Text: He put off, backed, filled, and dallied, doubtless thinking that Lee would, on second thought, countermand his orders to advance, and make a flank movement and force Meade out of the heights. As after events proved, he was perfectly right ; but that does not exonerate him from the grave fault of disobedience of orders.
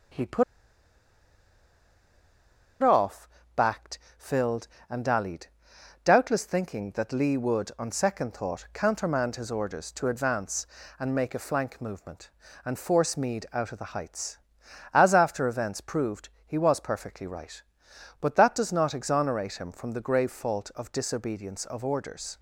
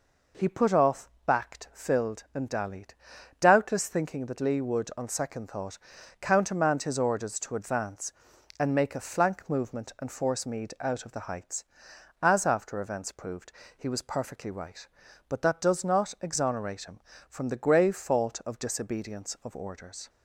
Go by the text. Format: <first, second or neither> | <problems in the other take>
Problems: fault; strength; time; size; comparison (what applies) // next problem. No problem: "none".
second | starts louder than the rest; until 3.7 s; 6.5 dB // pauses between "put" and "off"; strong; at 0.4 s; 2.3 s long